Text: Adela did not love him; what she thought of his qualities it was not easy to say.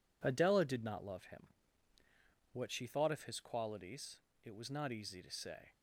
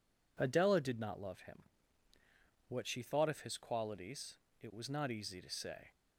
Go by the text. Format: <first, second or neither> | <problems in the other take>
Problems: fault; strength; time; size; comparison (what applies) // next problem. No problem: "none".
second | gets quieter; throughout; 7 dB // pauses between "qualities" and "it"; slight; at 4.1 s; 0.26 s long; slight in the second